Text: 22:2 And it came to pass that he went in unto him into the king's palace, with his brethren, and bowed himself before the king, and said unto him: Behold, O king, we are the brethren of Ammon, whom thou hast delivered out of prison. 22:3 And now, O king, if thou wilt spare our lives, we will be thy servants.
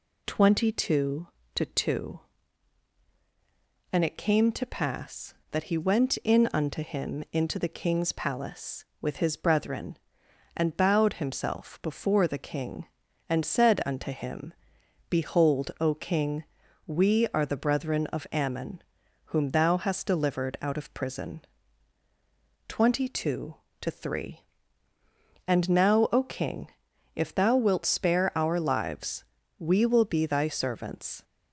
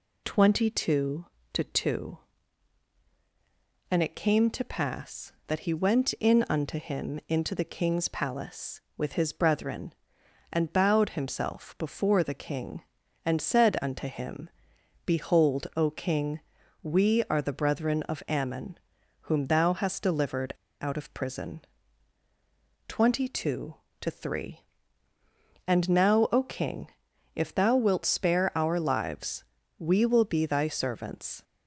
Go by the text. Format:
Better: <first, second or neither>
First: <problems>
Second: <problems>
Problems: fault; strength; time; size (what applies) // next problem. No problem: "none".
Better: first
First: none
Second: pauses between "delivered" and "out"; slight; at 20.5 s; 0.27 s long